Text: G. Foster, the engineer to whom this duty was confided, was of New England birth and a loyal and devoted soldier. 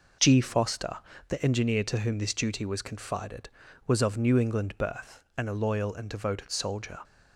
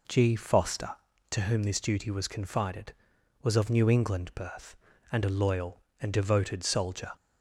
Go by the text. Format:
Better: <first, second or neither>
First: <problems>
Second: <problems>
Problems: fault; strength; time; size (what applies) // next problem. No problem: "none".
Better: first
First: none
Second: skips "the engineer"; at 1.1 s